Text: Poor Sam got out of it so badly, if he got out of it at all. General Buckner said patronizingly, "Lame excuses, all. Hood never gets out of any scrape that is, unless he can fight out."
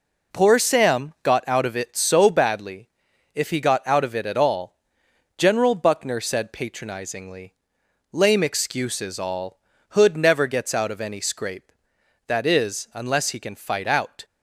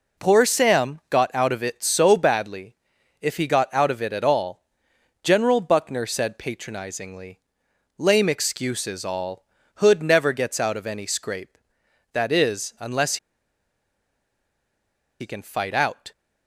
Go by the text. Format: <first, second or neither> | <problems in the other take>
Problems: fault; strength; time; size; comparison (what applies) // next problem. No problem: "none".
first | pauses between "unless" and "he"; strong; at 13.1 s; 2.0 s long